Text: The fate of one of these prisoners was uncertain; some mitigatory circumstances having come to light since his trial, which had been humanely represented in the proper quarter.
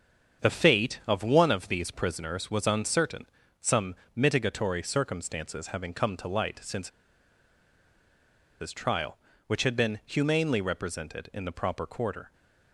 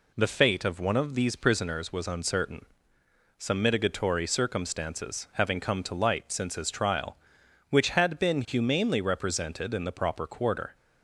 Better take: second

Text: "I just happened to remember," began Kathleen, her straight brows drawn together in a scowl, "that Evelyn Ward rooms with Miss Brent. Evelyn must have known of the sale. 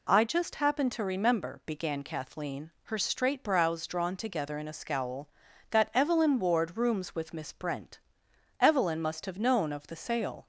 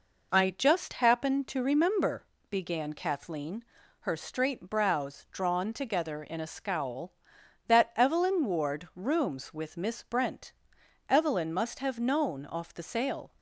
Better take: first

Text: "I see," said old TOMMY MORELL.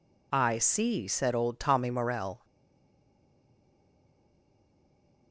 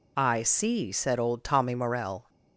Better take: second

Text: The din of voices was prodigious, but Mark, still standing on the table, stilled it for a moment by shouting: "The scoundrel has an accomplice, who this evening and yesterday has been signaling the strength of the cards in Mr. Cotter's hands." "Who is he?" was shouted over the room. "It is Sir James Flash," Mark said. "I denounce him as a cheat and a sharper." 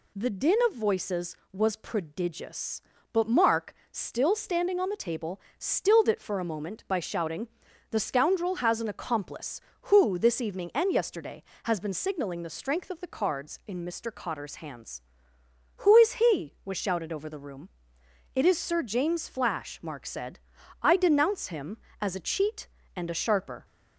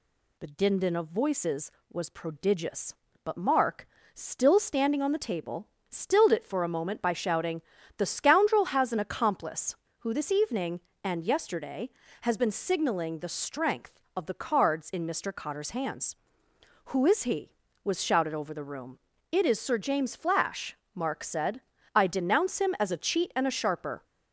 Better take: first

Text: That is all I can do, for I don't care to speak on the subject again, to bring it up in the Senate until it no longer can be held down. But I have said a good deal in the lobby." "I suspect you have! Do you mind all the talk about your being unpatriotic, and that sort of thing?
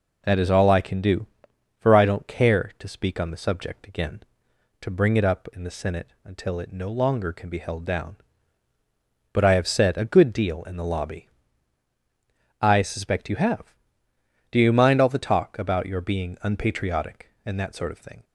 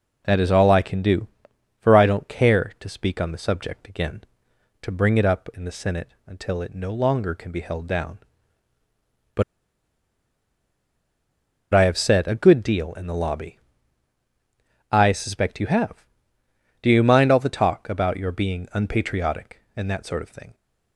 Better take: first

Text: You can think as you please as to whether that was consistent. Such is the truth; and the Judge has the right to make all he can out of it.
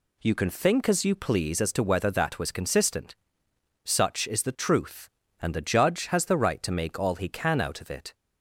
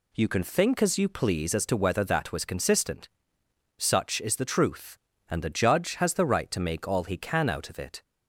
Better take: neither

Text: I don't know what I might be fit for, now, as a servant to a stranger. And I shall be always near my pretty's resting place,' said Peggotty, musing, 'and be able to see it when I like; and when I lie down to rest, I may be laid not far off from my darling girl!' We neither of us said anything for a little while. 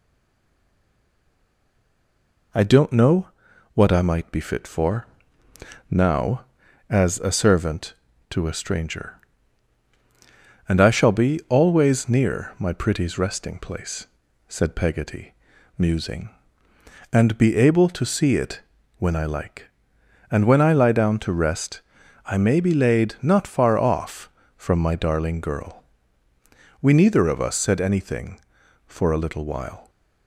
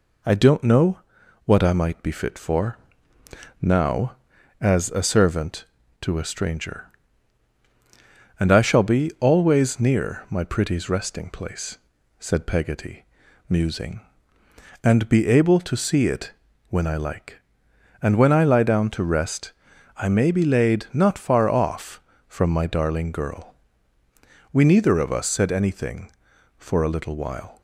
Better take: second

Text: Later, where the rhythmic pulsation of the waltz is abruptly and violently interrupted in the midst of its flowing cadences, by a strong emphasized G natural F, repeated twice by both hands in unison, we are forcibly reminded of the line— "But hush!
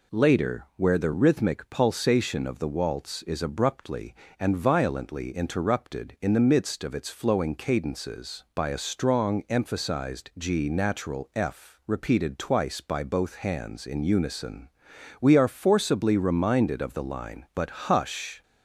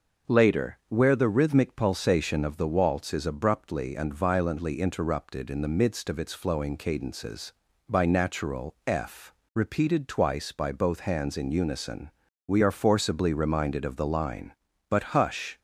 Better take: first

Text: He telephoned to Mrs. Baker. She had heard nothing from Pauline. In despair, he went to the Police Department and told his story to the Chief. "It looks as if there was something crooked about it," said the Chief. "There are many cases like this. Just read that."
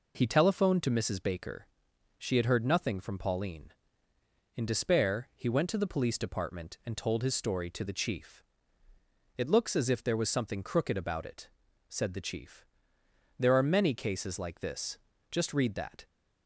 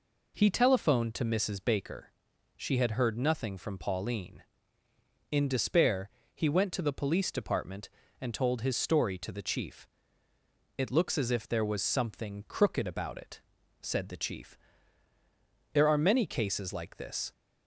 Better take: first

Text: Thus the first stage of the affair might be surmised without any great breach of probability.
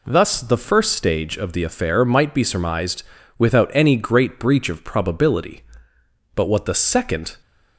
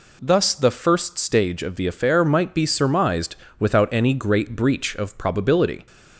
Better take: second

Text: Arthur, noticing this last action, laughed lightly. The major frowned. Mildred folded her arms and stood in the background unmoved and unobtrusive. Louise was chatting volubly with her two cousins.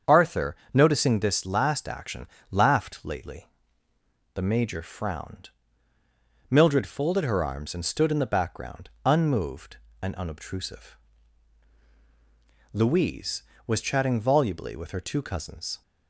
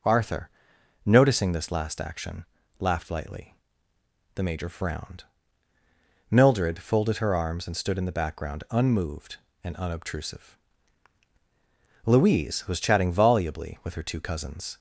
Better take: second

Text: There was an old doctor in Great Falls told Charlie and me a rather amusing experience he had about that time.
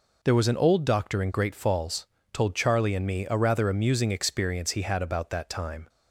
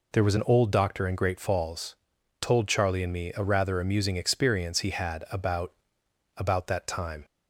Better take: first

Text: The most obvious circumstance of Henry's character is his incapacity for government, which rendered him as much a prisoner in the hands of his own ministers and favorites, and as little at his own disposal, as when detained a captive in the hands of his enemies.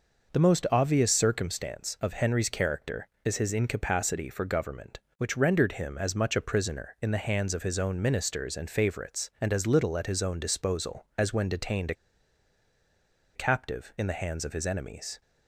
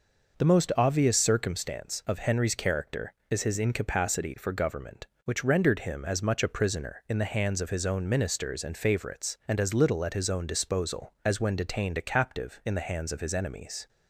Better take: second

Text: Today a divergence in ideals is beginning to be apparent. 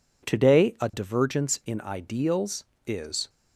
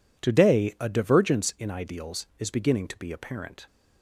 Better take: second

